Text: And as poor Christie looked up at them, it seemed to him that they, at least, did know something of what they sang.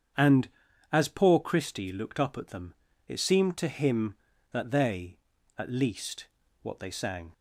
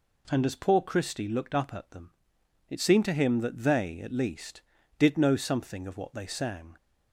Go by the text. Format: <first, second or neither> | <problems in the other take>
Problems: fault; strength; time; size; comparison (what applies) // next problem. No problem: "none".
second | starts louder than the rest; strong; until 1.5 s; 8 dB // skips "did know something of"; at 6.4 s